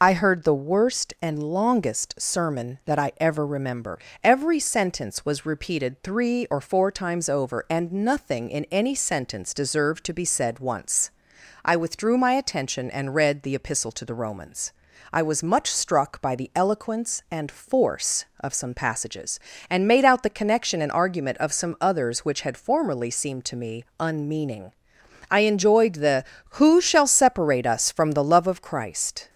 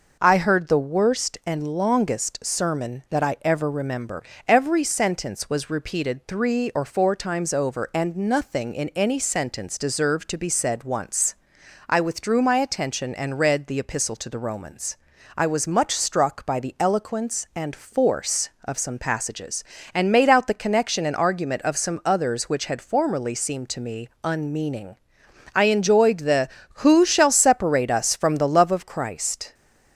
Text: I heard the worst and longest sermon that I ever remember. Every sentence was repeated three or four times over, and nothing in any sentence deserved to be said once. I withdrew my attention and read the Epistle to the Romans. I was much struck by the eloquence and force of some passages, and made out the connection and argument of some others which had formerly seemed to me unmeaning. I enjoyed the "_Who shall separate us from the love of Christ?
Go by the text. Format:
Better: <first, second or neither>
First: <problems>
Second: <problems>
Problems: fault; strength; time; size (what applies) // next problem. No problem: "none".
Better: second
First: loses the start of "I"; at 0.0 s; 60 ms // pauses between "me" and "unmeaning"; slight; at 23.8 s; 0.16 s long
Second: pauses between "me" and "unmeaning"; slight; at 24.0 s; 0.16 s long